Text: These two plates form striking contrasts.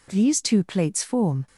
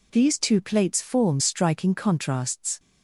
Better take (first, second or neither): second